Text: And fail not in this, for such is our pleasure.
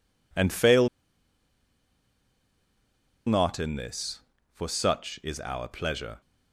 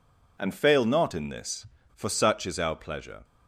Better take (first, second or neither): second